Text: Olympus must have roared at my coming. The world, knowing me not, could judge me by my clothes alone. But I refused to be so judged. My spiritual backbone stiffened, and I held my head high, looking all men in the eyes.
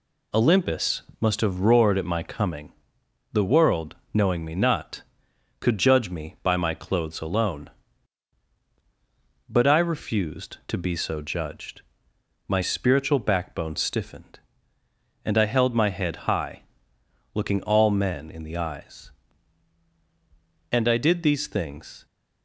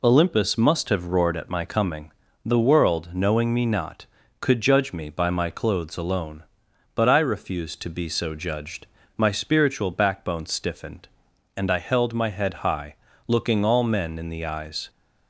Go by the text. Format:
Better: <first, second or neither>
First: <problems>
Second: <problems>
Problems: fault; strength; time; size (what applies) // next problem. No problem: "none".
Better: second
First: pauses between "Olympus" and "must"; slight; at 1.0 s; 0.18 s long // goes on to say "And I did these things"; from 20.7 s on; 1.3 s long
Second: none